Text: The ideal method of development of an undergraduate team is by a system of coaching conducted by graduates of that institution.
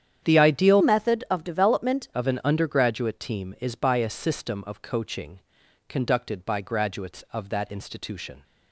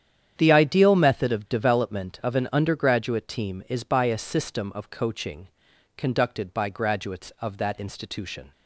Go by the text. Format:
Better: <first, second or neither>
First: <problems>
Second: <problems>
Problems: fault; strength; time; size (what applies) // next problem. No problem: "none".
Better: second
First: starts louder than the rest; strong; until 1.2 s; 9 dB // changes voice from "method" to "development"; from 0.8 to 2.0 s; 1.2 s long // pauses between "coaching" and "conducted"; noticeable; at 5.4 s; 0.48 s long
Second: starts louder than the rest; strong; until 1.3 s; 9 dB // pauses between "coaching" and "conducted"; noticeable; at 5.4 s; 0.48 s long